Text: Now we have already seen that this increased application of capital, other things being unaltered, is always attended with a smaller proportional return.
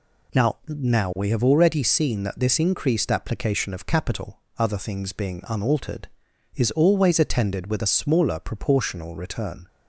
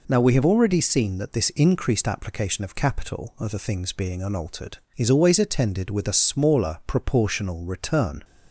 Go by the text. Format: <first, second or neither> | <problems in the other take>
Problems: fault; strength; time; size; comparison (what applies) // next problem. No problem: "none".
second | says "Now" twice; at 0.6 s